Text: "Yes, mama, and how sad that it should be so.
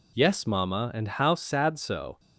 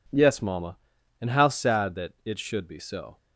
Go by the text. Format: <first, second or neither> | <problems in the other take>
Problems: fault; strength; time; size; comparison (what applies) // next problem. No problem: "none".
second | skips "that it should be"; at 1.7 s